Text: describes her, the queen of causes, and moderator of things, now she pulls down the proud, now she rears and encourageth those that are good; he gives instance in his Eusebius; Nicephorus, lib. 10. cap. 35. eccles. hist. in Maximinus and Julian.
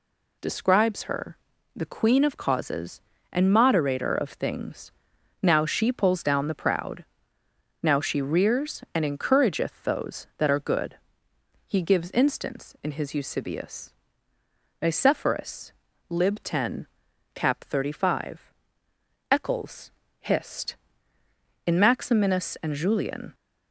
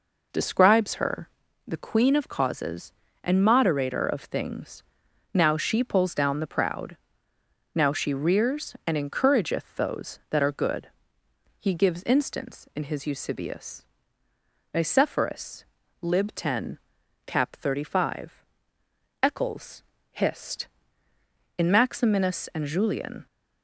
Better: first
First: none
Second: starts louder than the rest; noticeable; until 1.4 s; 4.5 dB

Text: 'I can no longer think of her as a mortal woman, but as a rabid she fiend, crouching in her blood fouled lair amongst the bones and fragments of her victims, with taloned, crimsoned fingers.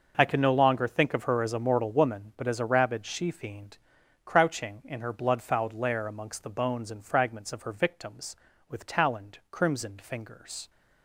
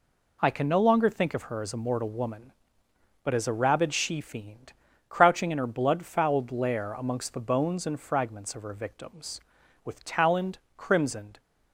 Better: first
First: none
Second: stops before "fingers"; at 11.3 s

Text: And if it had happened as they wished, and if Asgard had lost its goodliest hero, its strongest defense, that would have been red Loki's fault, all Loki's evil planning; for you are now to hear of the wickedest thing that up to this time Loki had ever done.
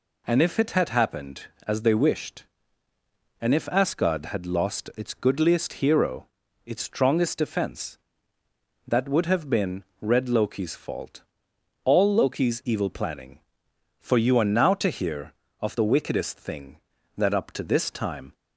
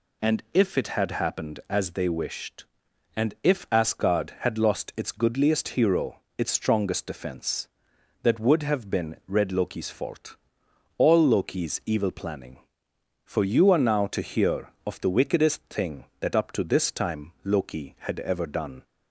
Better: second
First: pauses between "been" and "red"; slight; at 9.8 s; 0.18 s long // stops before "Loki had ever done"; at 18.3 s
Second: none

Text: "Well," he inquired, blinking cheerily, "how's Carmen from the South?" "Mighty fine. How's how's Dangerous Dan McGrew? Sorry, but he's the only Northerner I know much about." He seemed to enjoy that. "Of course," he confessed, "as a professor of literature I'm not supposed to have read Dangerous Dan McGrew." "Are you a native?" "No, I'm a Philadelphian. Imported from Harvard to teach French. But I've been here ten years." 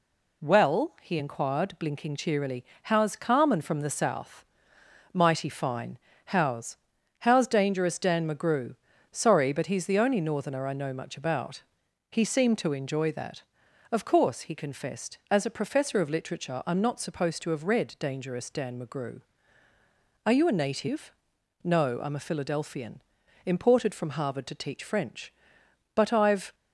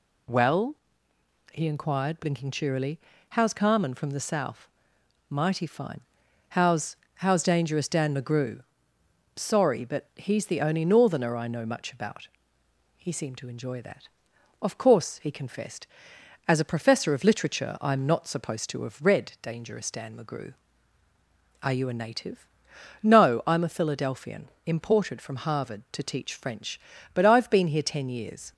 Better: second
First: pauses between "How's" and "how's"; at 6.7 s; 0.44 s long // stops before "been here ten years"; at 26.5 s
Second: pauses between "How's" and "how's"; slight; at 6.9 s; 0.20 s long

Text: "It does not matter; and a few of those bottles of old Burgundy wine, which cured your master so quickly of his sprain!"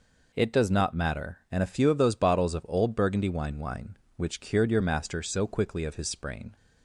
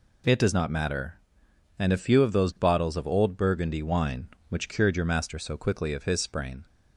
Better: second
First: says "wine" twice; at 3.5 s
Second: none

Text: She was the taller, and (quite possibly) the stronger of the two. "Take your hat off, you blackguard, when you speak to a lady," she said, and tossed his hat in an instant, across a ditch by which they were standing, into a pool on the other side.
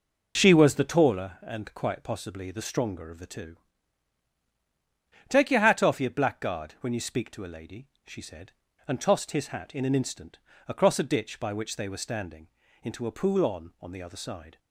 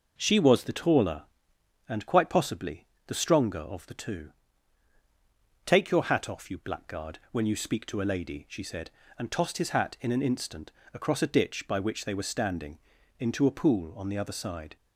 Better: second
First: says "on" twice; at 13.8 s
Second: none

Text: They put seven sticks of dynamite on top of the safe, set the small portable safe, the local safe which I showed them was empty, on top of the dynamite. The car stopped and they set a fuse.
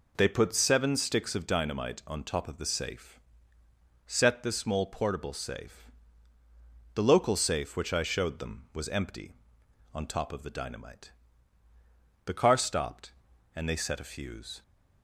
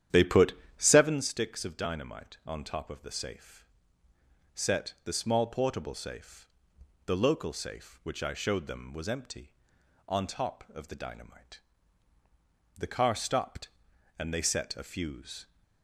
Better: first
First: none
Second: starts louder than the rest; strong; until 1.3 s; 10 dB // pauses between "put" and "seven"; slight; at 0.5 s; 0.26 s long

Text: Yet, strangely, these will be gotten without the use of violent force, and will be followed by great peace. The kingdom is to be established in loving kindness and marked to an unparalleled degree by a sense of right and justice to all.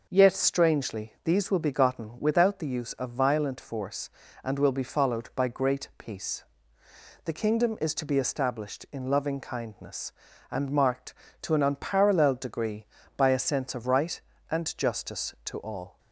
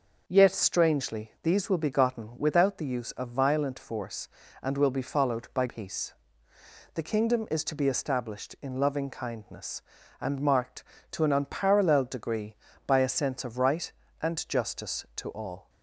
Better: first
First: none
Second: skips "great"; at 5.6 s

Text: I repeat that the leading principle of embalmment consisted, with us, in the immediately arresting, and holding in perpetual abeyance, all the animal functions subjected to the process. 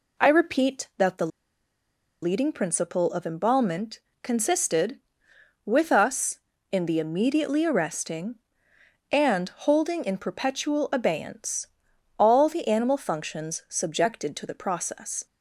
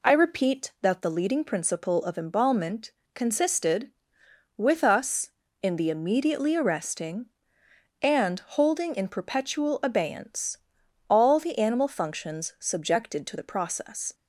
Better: second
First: pauses between "the" and "leading"; noticeable; at 1.2 s; 0.95 s long // pauses between "embalmment" and "consisted"; slight; at 3.9 s; 0.22 s long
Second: pauses between "embalmment" and "consisted"; slight; at 2.9 s; 0.22 s long

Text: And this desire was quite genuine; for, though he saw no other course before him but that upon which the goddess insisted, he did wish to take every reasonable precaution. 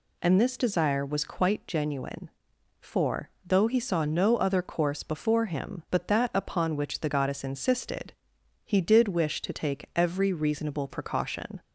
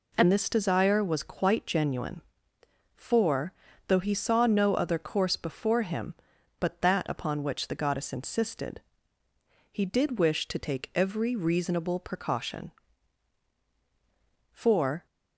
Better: first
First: none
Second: goes on to say "For"; from 14.5 s on; 0.54 s long

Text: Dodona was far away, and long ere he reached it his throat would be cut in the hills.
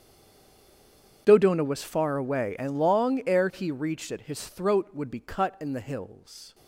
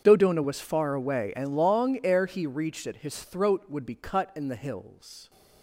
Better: second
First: stays silent before the first word; noticeable; until 1.2 s; 1.2 s long // starts louder than the rest; strong; until 2.2 s; 7.5 dB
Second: starts louder than the rest; strong; until 1.0 s; 7.5 dB

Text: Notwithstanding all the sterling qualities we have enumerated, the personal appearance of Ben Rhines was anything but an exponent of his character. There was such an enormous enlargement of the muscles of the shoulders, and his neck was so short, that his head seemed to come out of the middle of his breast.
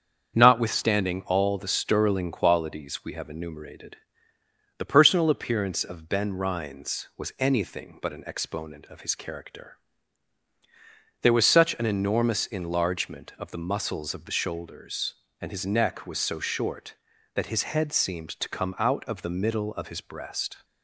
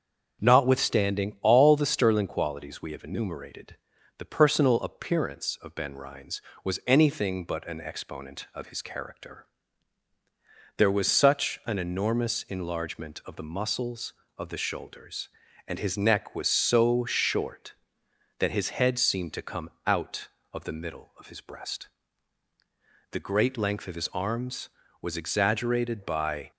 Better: first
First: starts louder than the rest; strong; until 1.4 s; 7.5 dB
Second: starts louder than the rest; until 1.4 s; 6.5 dB // pauses between "come" and "out"; slight; at 19.7 s; 0.16 s long // goes on to say "The great length of his arms was exaggerated by"; strong; from 23.1 s on; 3.3 s long

